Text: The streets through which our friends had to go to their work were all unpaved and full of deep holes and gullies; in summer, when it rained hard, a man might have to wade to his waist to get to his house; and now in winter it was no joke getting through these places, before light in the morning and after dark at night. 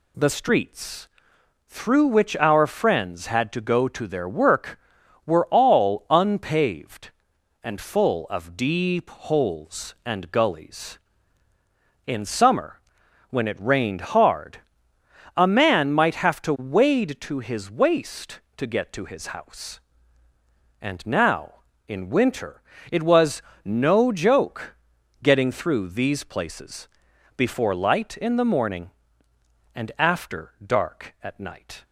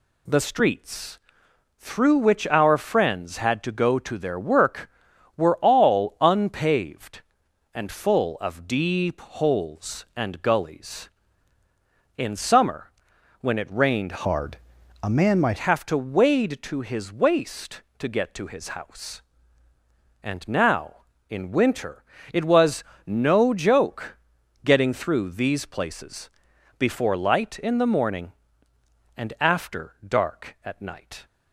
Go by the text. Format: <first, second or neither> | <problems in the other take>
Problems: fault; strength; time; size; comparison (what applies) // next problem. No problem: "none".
first | pauses between "streets" and "through"; noticeable; at 1.1 s; 0.60 s long; noticeable in the first // changes voice from "hard" to "might"; from 14.2 to 15.5 s; 1.3 s long // pauses between "winter" and "it"; slight; at 22.0 s; 0.30 s long; slight in the first // pauses between "was" and "no"; slight; at 22.8 s; 0.24 s long; slight in the first // pauses between "joke" and "getting"; noticeable; at 24.1 s; 0.48 s long; noticeable in the first